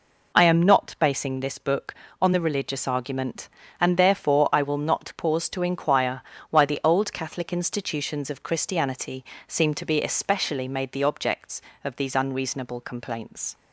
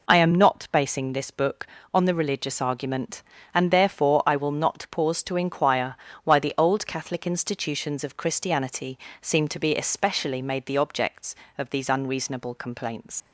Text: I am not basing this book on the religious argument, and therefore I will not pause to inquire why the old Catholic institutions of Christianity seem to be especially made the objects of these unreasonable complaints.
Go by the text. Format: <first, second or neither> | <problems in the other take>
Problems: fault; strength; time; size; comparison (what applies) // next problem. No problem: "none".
first | pauses between "inquire" and "why"; slight; at 5.9 s; 0.28 s long; slight in the first // pauses between "Christianity" and "seem"; slight; at 8.9 s; 0.24 s long; slight in the first // leaves "complaints" unfinished; at 13.2 s; 90 ms